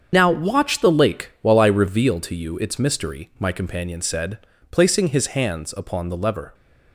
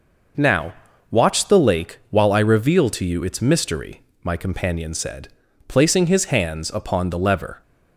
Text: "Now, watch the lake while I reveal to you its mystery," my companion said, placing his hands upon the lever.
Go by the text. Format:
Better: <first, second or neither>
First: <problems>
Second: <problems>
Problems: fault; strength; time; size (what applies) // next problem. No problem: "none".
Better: second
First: loses the start of "Now"; at 0.1 s; 65 ms // starts louder than the rest; strong; until 1.1 s; 7 dB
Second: none